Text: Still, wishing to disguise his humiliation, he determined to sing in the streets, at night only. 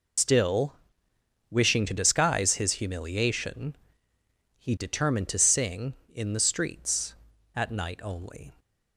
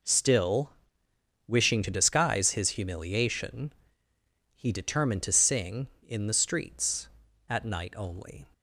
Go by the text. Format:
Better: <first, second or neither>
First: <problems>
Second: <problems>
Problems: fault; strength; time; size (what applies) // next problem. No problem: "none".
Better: second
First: loses the start of "Still"; at 0.1 s; 110 ms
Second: none